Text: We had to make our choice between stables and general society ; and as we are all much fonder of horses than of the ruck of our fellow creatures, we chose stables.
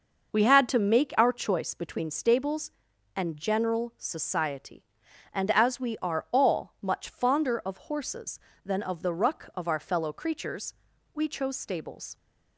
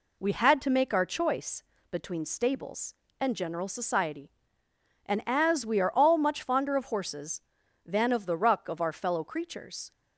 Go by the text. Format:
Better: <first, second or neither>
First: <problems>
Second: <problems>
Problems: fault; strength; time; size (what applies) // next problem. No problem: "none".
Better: first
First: none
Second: pauses between "choice" and "between"; slight; at 1.6 s; 0.30 s long // stops before "we chose stables"; at 9.9 s